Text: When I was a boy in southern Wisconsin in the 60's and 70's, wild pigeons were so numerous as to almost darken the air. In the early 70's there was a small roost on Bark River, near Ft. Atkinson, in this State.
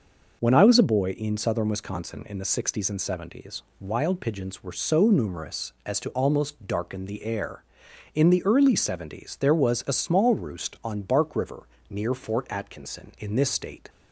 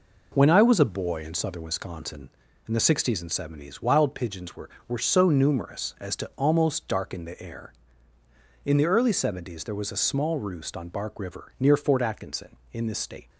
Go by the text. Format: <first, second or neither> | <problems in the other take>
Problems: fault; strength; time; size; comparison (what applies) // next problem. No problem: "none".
first | says "were" twice; at 4.8 s